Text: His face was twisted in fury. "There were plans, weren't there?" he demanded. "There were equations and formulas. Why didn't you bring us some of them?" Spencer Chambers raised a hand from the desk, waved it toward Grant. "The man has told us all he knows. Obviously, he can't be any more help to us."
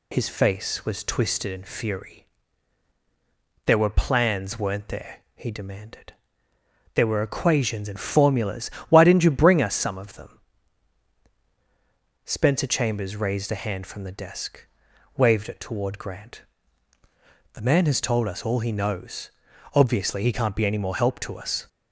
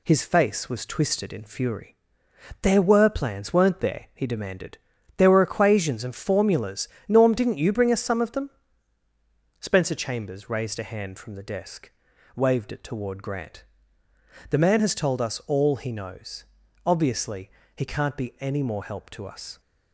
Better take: first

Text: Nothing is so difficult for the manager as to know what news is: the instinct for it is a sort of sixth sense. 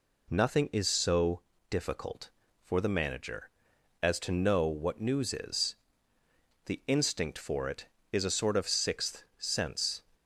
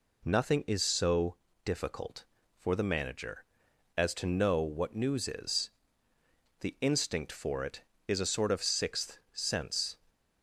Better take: neither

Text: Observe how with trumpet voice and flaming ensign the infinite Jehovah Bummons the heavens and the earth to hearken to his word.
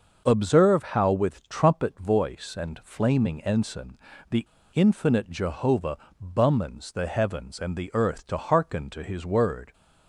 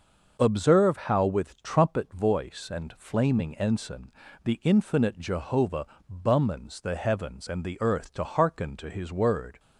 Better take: second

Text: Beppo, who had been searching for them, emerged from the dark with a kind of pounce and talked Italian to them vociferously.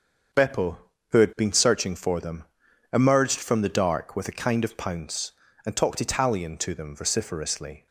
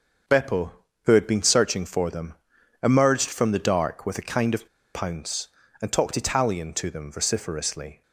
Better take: first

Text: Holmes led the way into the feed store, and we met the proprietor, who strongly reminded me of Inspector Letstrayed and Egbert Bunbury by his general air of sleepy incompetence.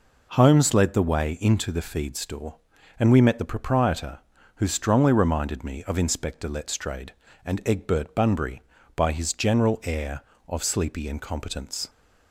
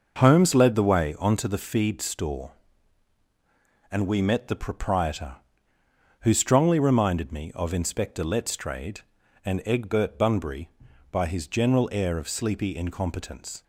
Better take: first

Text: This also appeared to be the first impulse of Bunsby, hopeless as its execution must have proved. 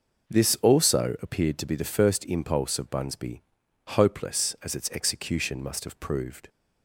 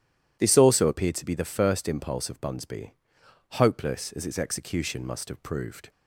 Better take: neither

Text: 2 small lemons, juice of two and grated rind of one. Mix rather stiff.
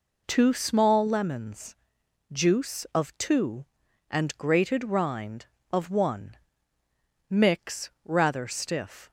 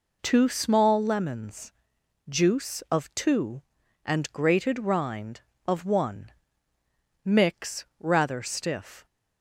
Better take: neither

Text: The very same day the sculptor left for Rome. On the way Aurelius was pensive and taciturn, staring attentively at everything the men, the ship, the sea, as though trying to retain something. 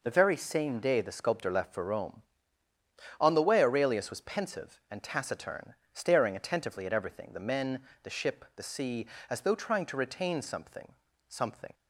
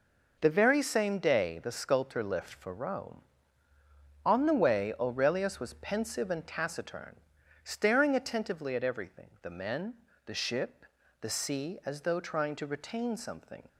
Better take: second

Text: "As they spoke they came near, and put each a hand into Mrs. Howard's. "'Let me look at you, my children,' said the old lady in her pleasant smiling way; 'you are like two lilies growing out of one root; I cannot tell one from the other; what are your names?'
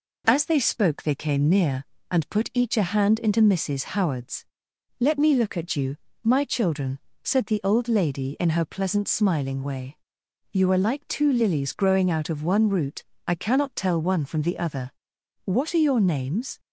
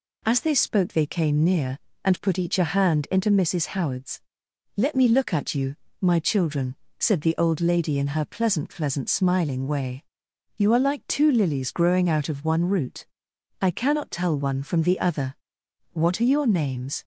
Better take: first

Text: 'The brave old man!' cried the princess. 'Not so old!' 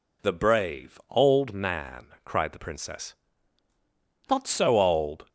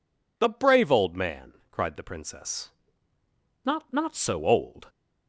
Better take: first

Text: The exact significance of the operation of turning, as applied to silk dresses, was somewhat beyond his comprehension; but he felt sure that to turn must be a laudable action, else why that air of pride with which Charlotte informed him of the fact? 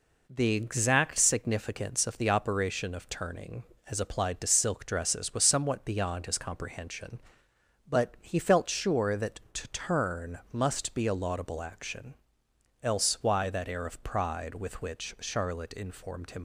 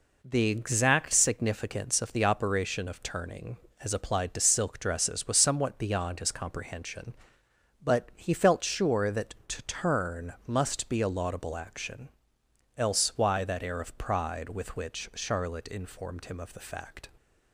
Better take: second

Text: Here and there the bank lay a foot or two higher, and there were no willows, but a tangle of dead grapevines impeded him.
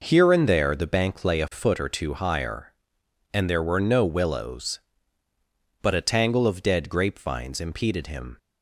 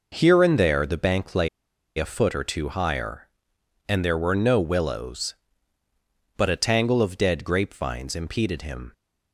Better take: first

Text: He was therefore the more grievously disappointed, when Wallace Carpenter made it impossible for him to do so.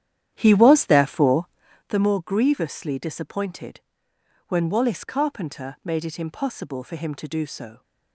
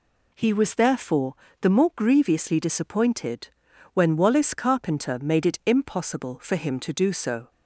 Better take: second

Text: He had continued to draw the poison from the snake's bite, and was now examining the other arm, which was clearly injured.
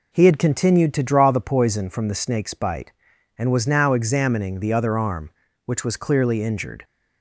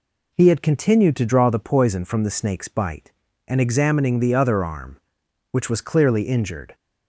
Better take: first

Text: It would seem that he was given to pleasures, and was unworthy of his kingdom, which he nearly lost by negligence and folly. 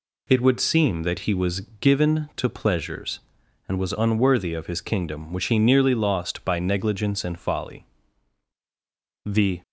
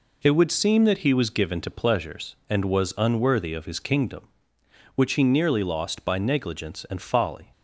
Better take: second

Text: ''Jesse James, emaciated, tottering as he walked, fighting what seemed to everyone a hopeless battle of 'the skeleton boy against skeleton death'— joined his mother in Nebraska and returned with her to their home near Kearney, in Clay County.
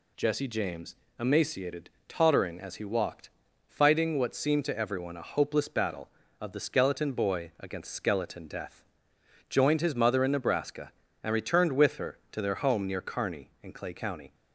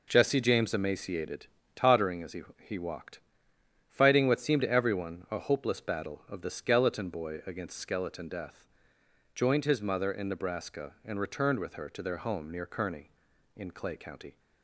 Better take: first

